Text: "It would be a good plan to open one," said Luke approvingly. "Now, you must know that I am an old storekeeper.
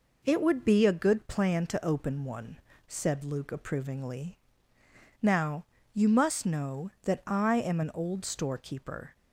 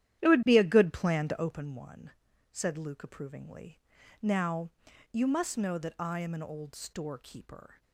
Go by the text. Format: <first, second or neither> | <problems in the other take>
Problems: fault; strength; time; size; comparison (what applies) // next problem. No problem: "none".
first | starts louder than the rest; strong; until 1.6 s; 11 dB